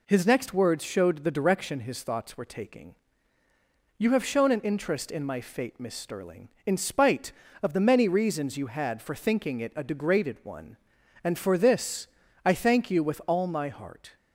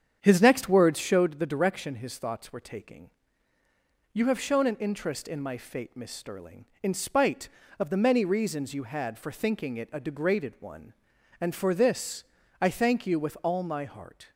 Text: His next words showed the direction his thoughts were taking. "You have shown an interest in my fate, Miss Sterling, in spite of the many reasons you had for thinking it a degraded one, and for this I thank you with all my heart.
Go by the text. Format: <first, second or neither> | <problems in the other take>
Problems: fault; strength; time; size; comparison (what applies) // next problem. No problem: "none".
first | starts louder than the rest; strong; until 1.4 s; 8 dB // pauses between "this" and "I"; at 12.2 s; 0.37 s long; also in the first